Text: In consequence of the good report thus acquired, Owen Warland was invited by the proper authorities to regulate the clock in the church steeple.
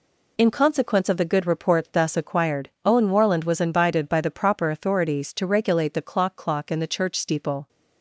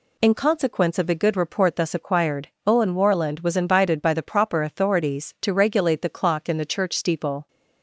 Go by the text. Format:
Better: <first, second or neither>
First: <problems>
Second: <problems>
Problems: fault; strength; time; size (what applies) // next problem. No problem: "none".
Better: second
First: says "clock" twice; at 6.3 s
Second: none